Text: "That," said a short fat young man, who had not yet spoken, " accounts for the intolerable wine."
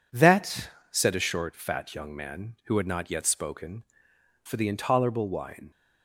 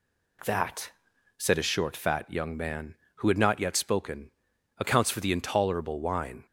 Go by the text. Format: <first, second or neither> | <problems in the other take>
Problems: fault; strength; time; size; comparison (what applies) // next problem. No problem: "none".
second | skips "accounts"; at 4.4 s